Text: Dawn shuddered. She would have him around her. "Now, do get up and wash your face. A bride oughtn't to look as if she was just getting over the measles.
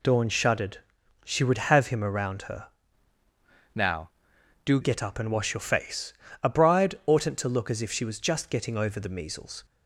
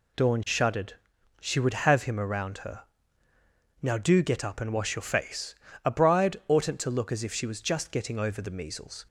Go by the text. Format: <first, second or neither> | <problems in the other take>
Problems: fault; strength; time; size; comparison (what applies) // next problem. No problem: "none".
second | changes voice from "Now" to "do"; from 3.7 to 4.8 s; 1.1 s long